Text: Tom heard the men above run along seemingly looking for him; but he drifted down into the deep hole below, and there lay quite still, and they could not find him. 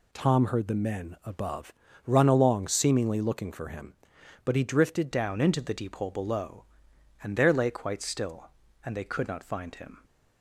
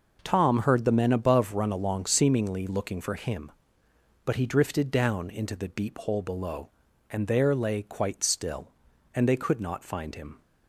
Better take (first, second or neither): second